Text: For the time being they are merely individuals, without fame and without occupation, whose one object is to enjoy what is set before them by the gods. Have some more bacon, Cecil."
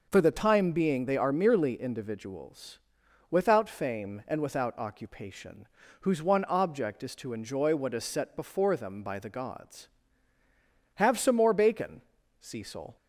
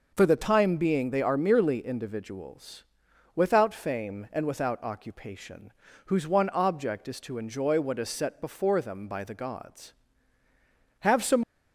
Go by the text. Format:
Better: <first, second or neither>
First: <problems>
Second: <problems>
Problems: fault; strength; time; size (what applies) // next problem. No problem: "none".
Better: first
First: none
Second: stops before "more bacon Cecil"; at 11.4 s